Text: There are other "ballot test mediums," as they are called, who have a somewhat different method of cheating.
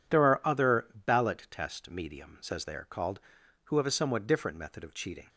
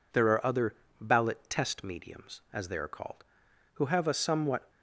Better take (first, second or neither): first